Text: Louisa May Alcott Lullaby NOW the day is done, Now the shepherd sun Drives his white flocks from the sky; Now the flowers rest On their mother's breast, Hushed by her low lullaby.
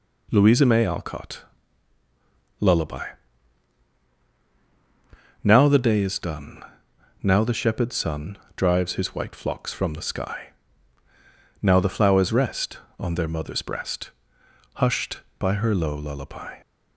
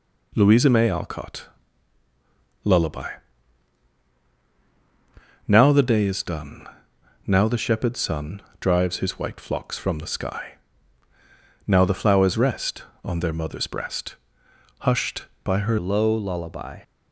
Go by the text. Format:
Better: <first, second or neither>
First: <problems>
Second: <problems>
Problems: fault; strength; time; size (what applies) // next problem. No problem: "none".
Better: first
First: pauses between "Alcott" and "Lullaby"; at 1.4 s; 1.1 s long // pauses between "Lullaby" and "NOW"; strong; at 3.0 s; 2.3 s long // pauses between "sun" and "Drives"; slight; at 8.3 s; 0.18 s long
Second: pauses between "Alcott" and "Lullaby"; at 1.4 s; 1.1 s long // pauses between "Lullaby" and "NOW"; strong; at 3.0 s; 2.3 s long // pauses between "sun" and "Drives"; slight; at 8.4 s; 0.18 s long // changes voice at "low"; from 15.7 s on; 1.1 s long